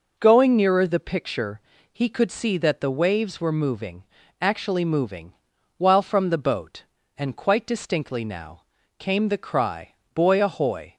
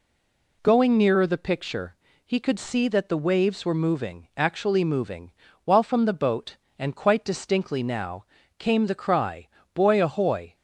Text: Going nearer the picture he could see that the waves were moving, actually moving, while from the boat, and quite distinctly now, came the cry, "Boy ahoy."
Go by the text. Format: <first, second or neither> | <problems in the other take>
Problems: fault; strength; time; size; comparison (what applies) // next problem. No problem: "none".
first | stays silent before the first word; slight; until 0.6 s; 0.6 s long // pauses between "picture" and "he"; slight; at 1.9 s; 0.30 s long; slight in the first